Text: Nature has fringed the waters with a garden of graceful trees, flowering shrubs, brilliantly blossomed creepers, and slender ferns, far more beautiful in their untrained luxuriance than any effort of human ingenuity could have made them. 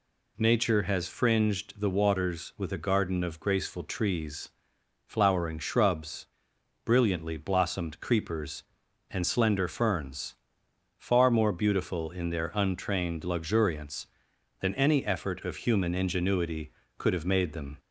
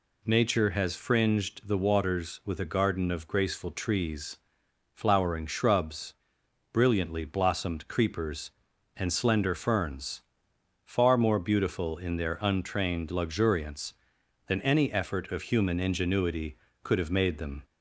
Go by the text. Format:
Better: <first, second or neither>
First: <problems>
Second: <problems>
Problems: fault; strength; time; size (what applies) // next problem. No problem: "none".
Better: neither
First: none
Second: none